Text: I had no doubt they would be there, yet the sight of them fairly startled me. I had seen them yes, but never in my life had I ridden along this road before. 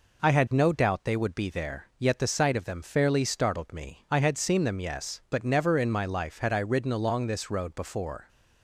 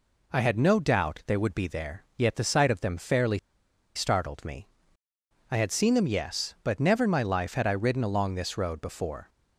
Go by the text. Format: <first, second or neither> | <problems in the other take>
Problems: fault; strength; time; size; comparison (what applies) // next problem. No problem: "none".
first | pauses between "fairly" and "startled"; noticeable; at 3.3 s; 0.58 s long